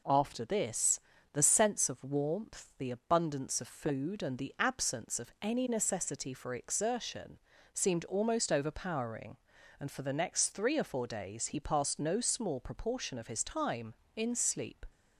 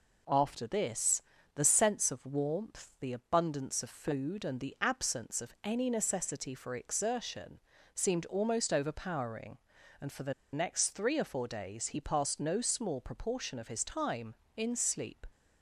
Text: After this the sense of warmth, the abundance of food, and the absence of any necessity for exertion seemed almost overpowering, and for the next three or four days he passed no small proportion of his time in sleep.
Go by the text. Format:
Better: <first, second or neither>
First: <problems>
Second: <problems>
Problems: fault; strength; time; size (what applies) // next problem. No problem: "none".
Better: first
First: pauses between "this" and "the"; slight; at 0.9 s; 0.34 s long // pauses between "exertion" and "seemed"; slight; at 7.3 s; 0.34 s long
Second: pauses between "this" and "the"; slight; at 1.2 s; 0.34 s long // pauses between "exertion" and "seemed"; slight; at 7.5 s; 0.34 s long // pauses between "the" and "next"; slight; at 10.3 s; 0.20 s long